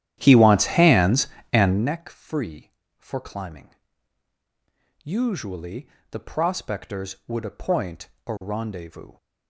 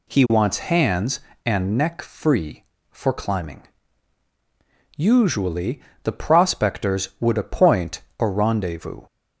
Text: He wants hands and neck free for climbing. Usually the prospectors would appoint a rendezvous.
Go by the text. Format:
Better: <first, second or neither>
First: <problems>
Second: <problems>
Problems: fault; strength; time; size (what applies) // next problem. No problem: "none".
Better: second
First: starts louder than the rest; strong; until 2.0 s; 11.5 dB // pauses between "Usually" and "the"; slight; at 5.8 s; 0.24 s long // pauses between "appoint" and "a"; slight; at 8.0 s; 0.18 s long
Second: pauses between "Usually" and "the"; slight; at 5.7 s; 0.24 s long // pauses between "appoint" and "a"; slight; at 8.0 s; 0.18 s long